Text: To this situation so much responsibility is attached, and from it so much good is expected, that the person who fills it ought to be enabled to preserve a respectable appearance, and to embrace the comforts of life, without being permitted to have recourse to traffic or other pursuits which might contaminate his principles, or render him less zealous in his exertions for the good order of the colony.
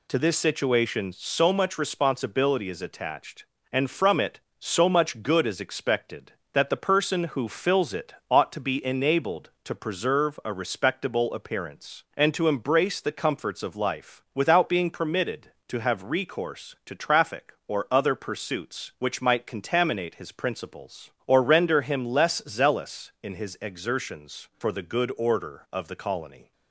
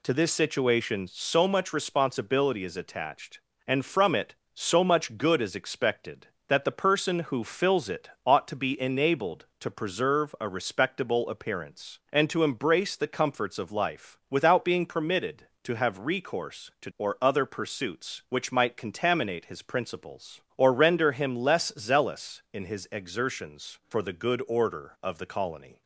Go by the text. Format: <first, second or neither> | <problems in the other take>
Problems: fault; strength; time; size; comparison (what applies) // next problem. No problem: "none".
first | pauses between "it" and "ought"; slight; at 8.0 s; 0.16 s long; slight in the first // skips "traffic"; at 16.9 s